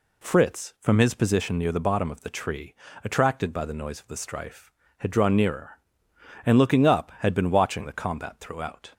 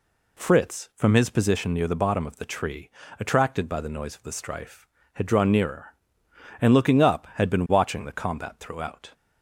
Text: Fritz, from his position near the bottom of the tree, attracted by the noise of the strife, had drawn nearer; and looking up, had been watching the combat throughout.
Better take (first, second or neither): neither